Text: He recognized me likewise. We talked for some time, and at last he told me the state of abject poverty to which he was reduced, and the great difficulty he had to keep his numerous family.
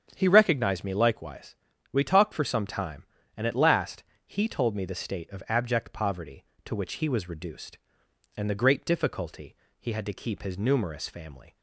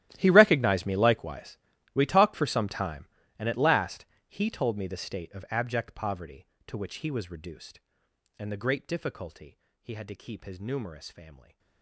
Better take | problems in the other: first | gets quieter; strong; throughout; 19.5 dB // starts louder than the rest; strong; until 1.1 s; 14 dB; strong in the first // pauses between "last" and "he"; slight; at 4.0 s; 0.22 s long; slight in the first // pauses between "difficulty" and "he"; slight; at 9.5 s; 0.26 s long; slight in the first

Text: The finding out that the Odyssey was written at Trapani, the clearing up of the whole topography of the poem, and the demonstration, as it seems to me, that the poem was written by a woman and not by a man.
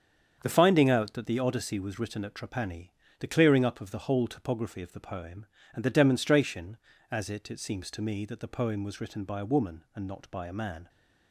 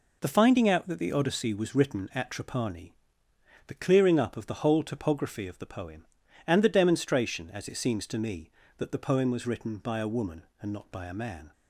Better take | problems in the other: second | starts louder than the rest; strong; until 1.4 s; 7.5 dB // says "it" twice; at 7.5 s

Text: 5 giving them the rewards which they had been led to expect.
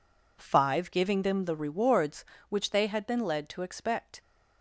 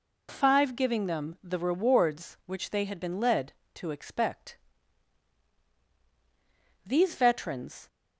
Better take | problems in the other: first | goes on to say "These veterans"; noticeable; from 6.8 s on; 1.0 s long

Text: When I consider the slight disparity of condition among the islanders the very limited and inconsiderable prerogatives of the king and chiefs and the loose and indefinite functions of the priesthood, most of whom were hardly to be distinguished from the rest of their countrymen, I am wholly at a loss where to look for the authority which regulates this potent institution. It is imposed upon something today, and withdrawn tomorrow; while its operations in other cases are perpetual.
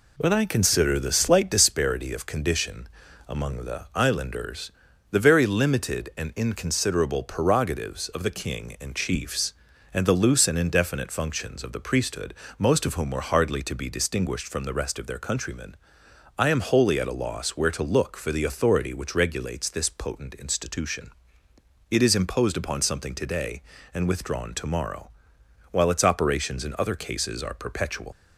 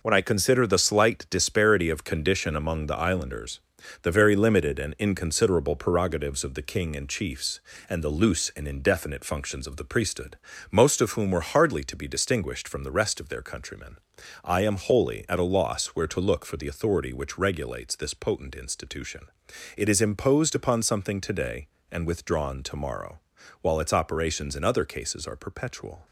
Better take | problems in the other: second | pauses between "condition" and "among"; at 2.8 s; 0.40 s long // pauses between "islanders" and "the"; at 4.7 s; 0.38 s long; also in the second // leaves "perpetual" unfinished; at 28.1 s; 95 ms

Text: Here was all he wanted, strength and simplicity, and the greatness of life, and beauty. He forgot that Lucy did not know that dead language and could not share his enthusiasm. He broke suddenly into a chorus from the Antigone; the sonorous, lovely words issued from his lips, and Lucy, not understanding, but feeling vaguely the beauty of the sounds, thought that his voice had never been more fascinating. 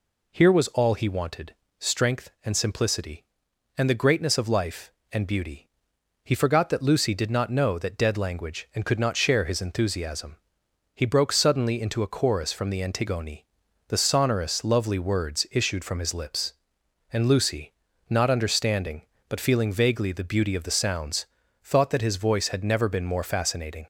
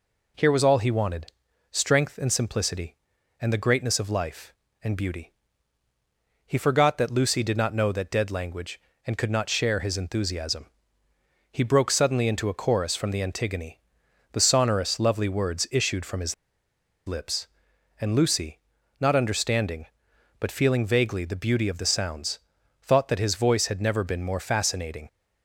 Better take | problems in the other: first | pauses between "his" and "lips"; noticeable; at 16.3 s; 0.73 s long

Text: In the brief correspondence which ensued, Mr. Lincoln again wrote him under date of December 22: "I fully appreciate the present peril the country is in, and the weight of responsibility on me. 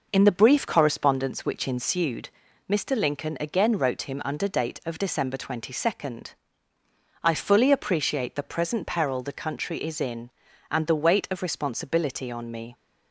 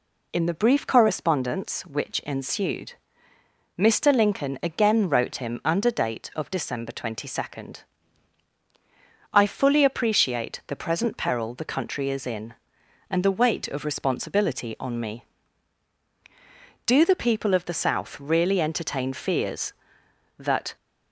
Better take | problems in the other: first | goes on to say "Do the people of the South really entertain fears that"; strong; from 16.8 s on; 3.9 s long

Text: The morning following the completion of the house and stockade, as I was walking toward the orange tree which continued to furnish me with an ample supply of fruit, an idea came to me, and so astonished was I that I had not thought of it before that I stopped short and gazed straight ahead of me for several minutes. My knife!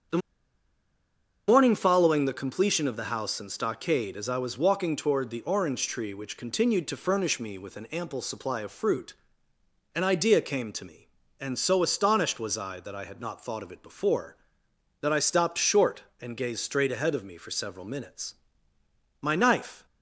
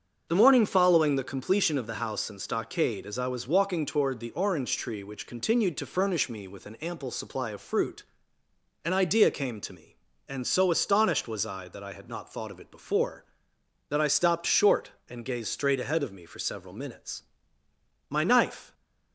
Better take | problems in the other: second | starts louder than the rest; strong; until 2.4 s; 7.5 dB; strong in the second // pauses between "The" and "morning"; strong; at 0.2 s; 1.2 s long

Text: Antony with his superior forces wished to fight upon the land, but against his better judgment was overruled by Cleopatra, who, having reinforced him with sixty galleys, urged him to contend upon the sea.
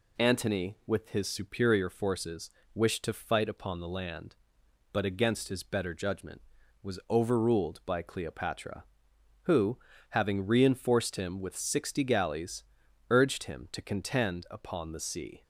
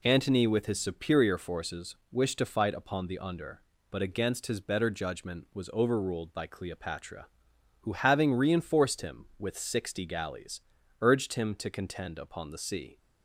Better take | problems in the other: first | pauses between "forces" and "wished"; slight; at 1.9 s; 0.16 s long; slight in the first // says "under" for "land"; at 3.1 s

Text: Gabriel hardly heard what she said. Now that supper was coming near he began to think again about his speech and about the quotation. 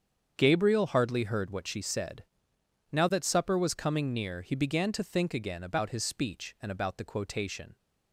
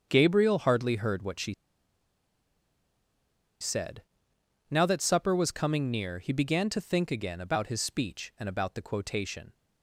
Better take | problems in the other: first | starts louder than the rest; strong; until 1.1 s; 7.5 dB; strong in the first // pauses between "she" and "said"; strong; at 1.5 s; 2.0 s long

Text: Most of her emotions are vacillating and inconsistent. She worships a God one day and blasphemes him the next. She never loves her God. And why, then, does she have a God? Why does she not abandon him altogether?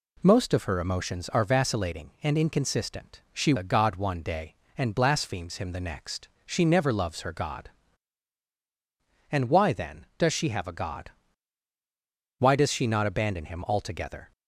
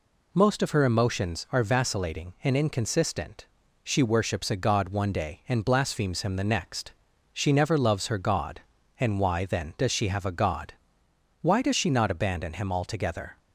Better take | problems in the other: second | skips "worships"; at 3.5 s

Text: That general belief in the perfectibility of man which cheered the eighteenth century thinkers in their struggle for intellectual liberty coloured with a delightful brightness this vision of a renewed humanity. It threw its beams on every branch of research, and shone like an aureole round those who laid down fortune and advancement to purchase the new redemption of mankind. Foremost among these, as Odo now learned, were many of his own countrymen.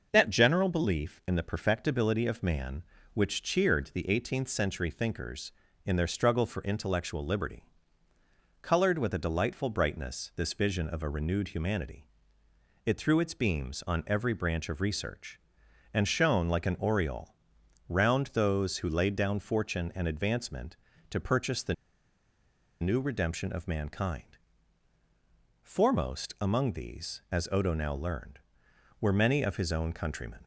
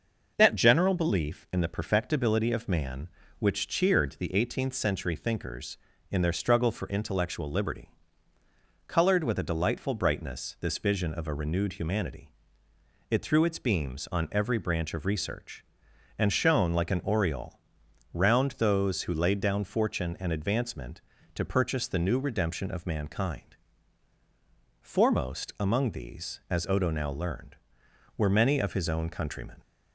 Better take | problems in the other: second | pauses between "liberty" and "coloured"; noticeable; at 7.6 s; 0.98 s long; noticeable in the second // pauses between "aureole" and "round"; noticeable; at 17.3 s; 0.52 s long; noticeable in the second // pauses between "the" and "new"; at 21.7 s; 1.0 s long

